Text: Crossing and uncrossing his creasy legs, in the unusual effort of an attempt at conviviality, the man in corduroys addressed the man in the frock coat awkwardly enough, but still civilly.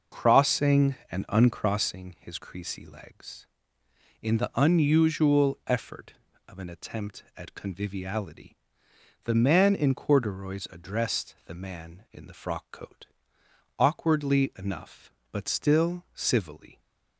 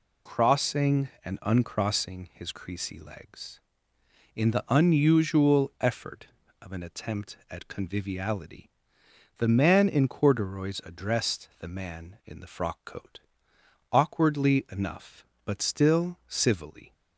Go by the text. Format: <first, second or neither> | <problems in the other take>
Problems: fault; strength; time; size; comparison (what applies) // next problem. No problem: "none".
second | starts louder than the rest; noticeable; until 1.8 s; 5.5 dB // pauses between "coat" and "awkwardly"; noticeable; at 13.0 s; 0.72 s long; noticeable in the second